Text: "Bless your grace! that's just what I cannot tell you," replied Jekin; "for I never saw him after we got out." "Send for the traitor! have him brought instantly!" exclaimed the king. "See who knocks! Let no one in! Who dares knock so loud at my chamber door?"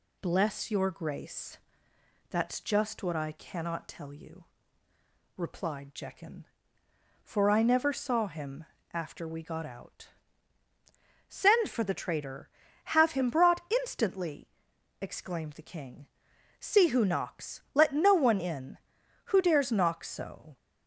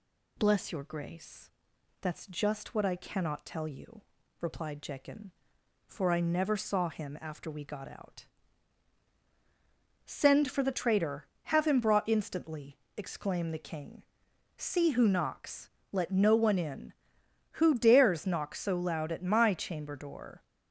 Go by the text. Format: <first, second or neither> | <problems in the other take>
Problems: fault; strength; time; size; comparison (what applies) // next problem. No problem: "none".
second | pauses between "him" and "after"; slight; at 8.6 s; 0.28 s long // stops before "loud at my chamber door"; at 20.5 s